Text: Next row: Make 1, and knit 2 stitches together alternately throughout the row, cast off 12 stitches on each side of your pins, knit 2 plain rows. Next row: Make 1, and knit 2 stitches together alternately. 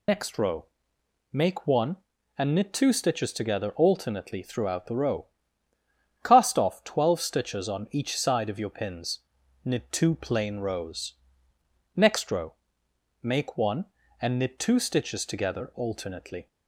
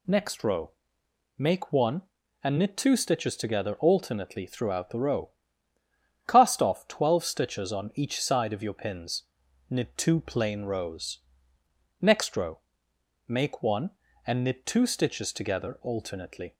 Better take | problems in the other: second | loses the start of "Next"; at 0.0 s; 70 ms

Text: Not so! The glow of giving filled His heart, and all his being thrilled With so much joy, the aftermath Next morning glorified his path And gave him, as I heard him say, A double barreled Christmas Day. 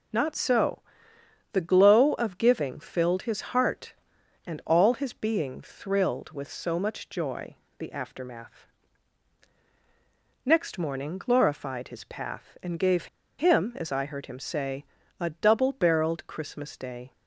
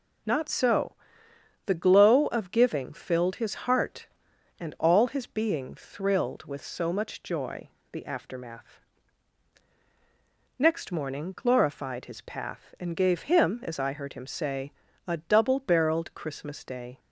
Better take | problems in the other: second | pauses between "aftermath" and "Next"; strong; at 8.6 s; 1.8 s long; strong in the second // pauses between "gave" and "him"; slight; at 13.0 s; 0.32 s long

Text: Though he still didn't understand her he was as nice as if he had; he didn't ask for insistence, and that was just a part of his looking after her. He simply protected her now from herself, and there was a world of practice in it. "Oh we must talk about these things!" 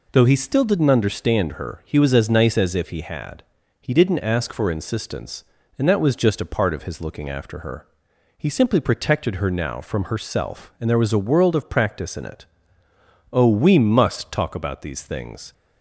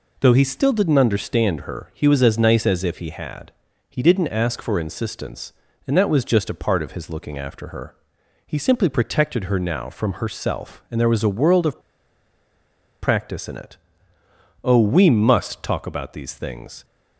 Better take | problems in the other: first | pauses between "of" and "practice"; at 11.7 s; 1.2 s long

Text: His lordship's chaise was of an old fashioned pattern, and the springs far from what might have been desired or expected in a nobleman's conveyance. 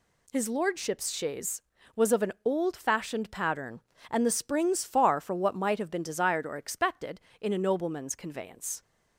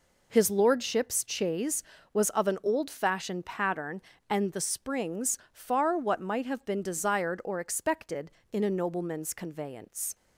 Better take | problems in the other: first | skips "from"; at 5.9 s

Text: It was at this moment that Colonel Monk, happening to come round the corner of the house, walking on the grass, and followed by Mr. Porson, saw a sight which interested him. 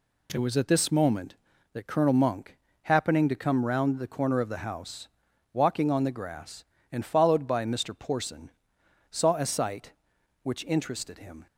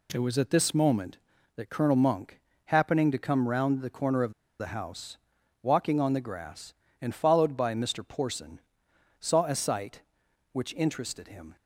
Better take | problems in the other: first | pauses between "of" and "the"; slight; at 4.3 s; 0.26 s long

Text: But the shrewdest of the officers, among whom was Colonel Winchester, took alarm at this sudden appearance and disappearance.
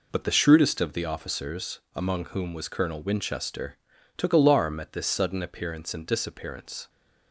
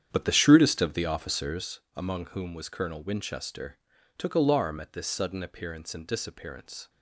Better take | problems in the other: first | starts louder than the rest; strong; until 1.7 s; 9 dB

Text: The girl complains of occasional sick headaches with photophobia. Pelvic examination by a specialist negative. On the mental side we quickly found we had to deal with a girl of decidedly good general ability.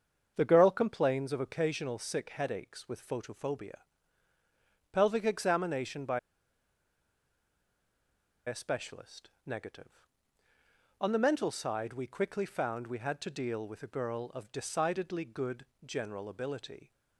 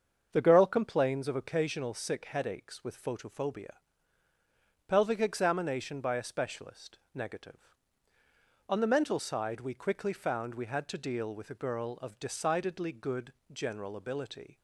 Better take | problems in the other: second | starts louder than the rest; until 1.3 s; 7 dB; also in the second // pauses between "by" and "a"; strong; at 6.1 s; 2.2 s long // pauses between "specialist" and "negative"; slight; at 9.2 s; 0.16 s long; slight in the second // pauses between "good" and "general"; slight; at 15.6 s; 0.22 s long; slight in the second

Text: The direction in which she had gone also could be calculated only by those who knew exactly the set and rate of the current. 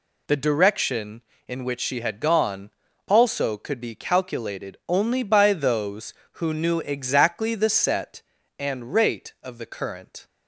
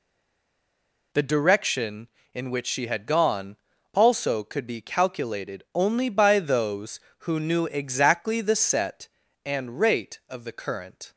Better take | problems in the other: first | stays silent before the first word; until 1.1 s; 1.1 s long // pauses between "gone" and "also"; at 3.5 s; 0.38 s long; also in the first

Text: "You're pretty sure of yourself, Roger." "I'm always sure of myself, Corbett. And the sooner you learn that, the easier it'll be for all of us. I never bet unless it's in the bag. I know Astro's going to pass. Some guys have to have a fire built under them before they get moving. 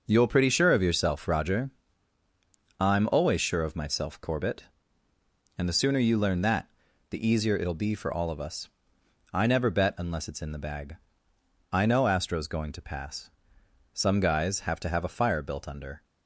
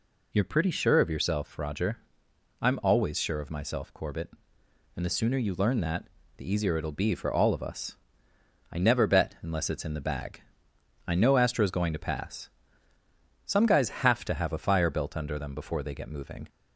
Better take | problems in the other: second | stops before "them before they get moving"; at 16.0 s

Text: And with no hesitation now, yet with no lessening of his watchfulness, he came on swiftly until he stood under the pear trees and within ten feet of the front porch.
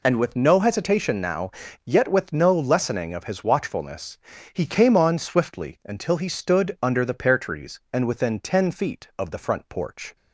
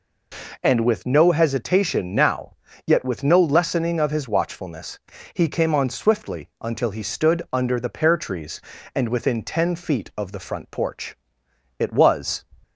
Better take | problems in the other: first | goes on to say "It was"; noticeable; from 11.8 s on; 0.64 s long

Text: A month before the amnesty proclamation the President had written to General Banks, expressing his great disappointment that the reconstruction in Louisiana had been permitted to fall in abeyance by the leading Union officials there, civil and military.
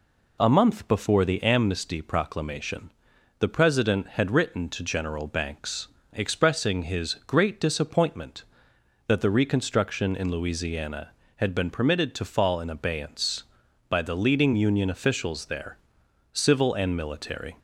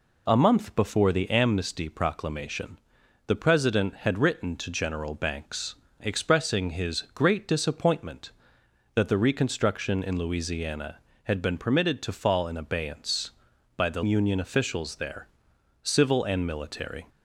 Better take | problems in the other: first | pauses between "proclamation" and "the"; noticeable; at 2.7 s; 0.48 s long; noticeable in the first // skips "leading"; at 14.0 s

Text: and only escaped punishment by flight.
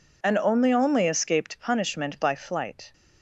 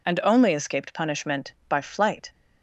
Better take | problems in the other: second | says "only" twice; at 0.7 s

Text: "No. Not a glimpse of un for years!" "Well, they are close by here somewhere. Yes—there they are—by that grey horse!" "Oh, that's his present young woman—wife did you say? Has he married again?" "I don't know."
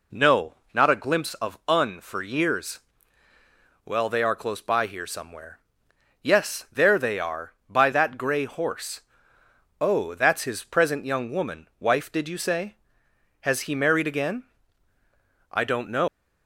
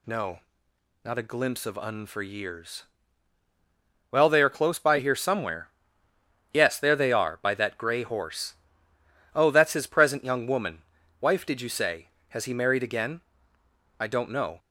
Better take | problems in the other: second | leaves "know" unfinished; at 16.0 s; 120 ms

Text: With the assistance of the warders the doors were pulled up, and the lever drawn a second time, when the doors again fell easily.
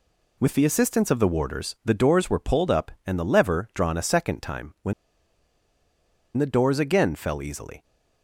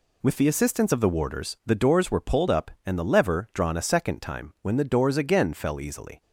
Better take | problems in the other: second | pauses between "when" and "the"; strong; at 4.9 s; 1.4 s long

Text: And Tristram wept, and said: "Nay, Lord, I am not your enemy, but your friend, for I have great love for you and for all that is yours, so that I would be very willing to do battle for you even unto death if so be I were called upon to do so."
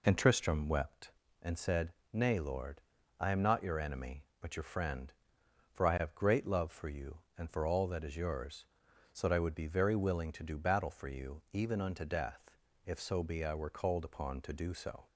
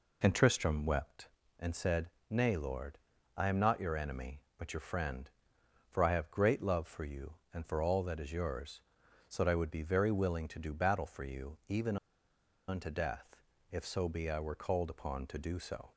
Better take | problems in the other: first | pauses between "even" and "unto"; noticeable; at 11.9 s; 0.72 s long // pauses between "death" and "if"; slight; at 13.4 s; 0.28 s long; slight in the first

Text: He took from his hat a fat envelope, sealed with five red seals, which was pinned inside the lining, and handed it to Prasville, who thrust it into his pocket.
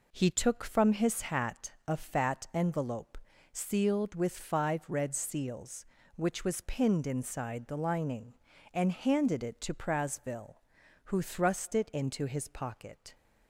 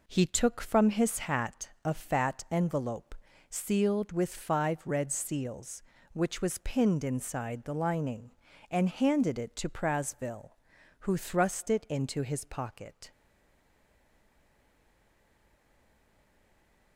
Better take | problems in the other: first | stays silent after the last word; strong; from 13.1 s on; 3.8 s long

